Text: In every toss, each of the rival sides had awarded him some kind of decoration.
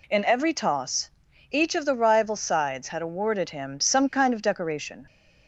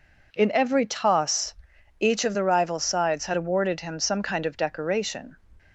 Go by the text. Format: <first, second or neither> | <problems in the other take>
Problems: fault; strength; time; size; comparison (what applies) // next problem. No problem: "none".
neither | none